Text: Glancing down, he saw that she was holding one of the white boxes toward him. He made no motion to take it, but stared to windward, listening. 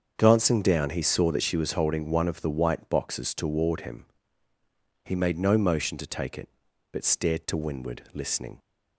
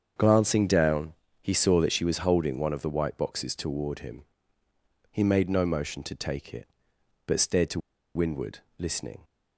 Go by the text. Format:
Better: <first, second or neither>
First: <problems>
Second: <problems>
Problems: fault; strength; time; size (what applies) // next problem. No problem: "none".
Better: first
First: starts louder than the rest; until 1.1 s; 7 dB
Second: starts louder than the rest; strong; until 1.4 s; 7 dB // pauses between "to" and "windward"; slight; at 7.7 s; 0.35 s long